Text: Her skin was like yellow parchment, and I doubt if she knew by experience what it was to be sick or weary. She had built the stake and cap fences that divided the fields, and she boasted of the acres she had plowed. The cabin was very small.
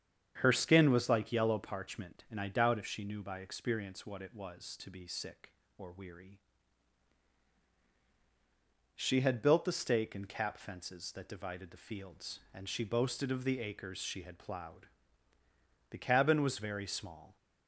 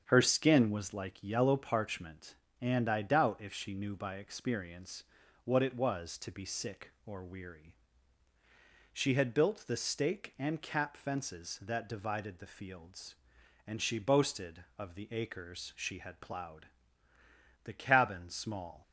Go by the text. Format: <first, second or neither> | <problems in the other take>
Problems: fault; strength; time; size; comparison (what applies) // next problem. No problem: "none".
first | starts louder than the rest; strong; until 1.0 s; 7.5 dB; strong in the first // pauses between "experience" and "what"; at 5.0 s; 0.42 s long // skips "was very"; at 18.2 s